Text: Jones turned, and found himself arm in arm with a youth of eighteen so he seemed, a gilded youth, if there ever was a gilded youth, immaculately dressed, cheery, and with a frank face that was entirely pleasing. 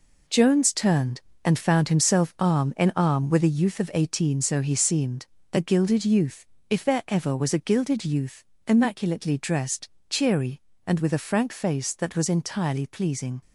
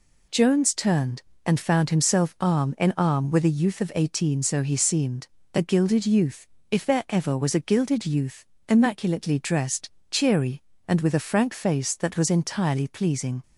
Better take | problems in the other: second | gets quieter; strong; throughout; 8 dB

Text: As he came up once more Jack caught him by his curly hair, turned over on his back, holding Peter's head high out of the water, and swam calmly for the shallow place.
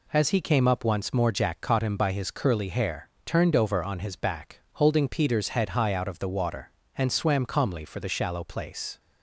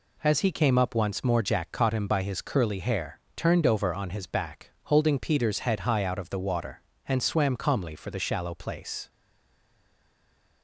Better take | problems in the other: first | stays silent after the last word; noticeable; from 9.1 s on; 1.5 s long

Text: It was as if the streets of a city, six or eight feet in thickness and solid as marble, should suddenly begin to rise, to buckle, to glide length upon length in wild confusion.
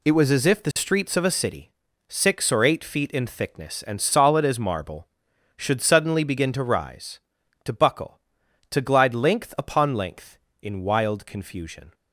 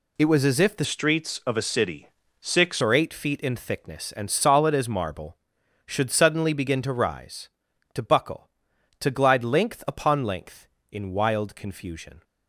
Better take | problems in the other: first | changes voice from "streets" to "six"; from 0.8 to 2.8 s; 2.0 s long

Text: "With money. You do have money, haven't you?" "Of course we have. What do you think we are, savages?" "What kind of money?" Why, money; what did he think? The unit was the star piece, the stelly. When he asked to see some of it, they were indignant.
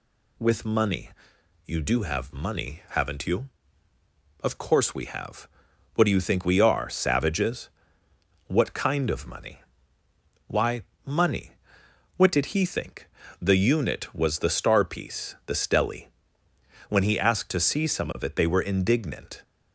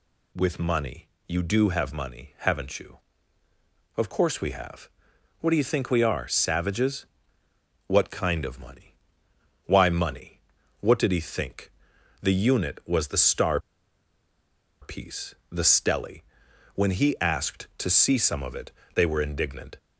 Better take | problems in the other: first | pauses between "star" and "piece"; at 13.5 s; 1.2 s long

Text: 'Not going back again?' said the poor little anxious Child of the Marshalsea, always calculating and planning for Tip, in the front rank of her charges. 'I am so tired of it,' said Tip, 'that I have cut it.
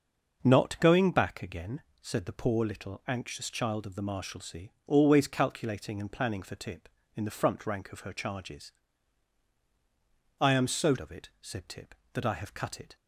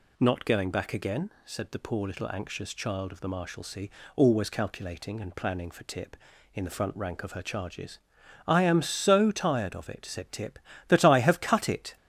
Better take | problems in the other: second | starts louder than the rest; until 1.4 s; 6 dB // skips "tired"; at 10.9 s

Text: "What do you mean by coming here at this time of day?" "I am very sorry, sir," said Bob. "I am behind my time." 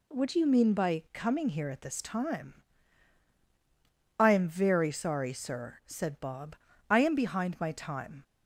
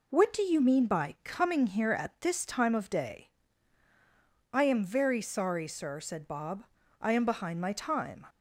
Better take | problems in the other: second | skips "of day"; at 3.3 s

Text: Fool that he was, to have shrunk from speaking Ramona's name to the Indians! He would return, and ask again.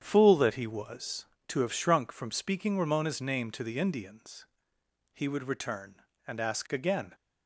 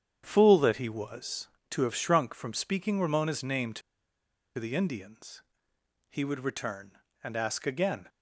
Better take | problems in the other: first | starts louder than the rest; strong; until 1.2 s; 8.5 dB; strong in the first // pauses between "to" and "the"; noticeable; at 3.8 s; 0.77 s long

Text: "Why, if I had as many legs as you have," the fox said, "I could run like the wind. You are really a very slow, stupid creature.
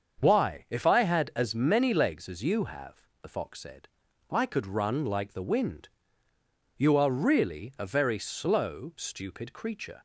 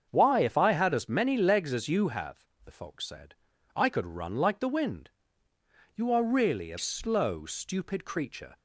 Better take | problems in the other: first | starts louder than the rest; strong; until 1.1 s; 7 dB; also in the first // skips "very"; at 6.7 s

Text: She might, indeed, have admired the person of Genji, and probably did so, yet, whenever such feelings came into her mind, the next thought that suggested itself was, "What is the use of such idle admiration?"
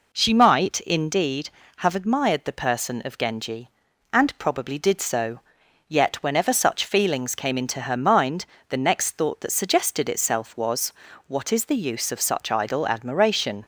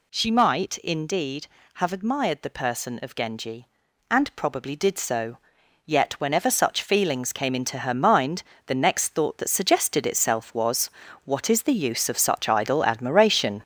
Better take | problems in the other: first | gets louder; throughout; 6.5 dB

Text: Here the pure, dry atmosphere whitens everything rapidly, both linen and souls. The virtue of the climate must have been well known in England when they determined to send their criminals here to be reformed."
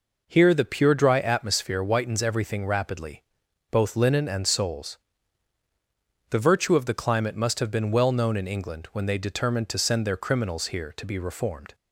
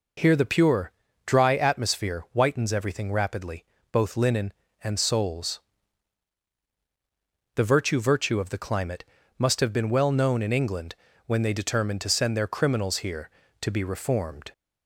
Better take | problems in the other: first | says "virtue" twice; at 8.0 s // pauses between "climate" and "must"; slight; at 9.0 s; 0.34 s long // pauses between "England" and "when"; slight; at 10.9 s; 0.30 s long

